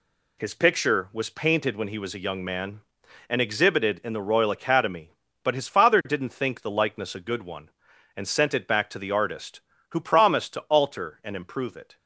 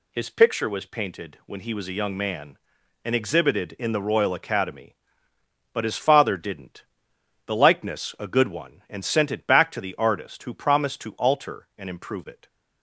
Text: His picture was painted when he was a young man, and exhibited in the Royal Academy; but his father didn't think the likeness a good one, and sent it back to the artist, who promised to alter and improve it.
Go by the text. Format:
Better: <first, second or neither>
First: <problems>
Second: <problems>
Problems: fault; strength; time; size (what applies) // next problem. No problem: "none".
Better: first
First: none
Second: skips "think"; at 7.1 s